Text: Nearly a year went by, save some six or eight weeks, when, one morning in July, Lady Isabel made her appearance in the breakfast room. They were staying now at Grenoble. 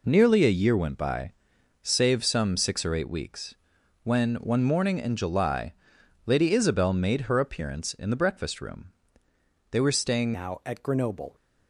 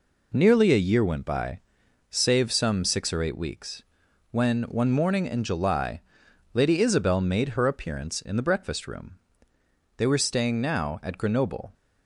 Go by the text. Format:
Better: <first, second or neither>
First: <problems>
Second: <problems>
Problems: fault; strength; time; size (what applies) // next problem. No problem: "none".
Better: second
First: changes voice at "now"; from 10.3 s on; 1.0 s long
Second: none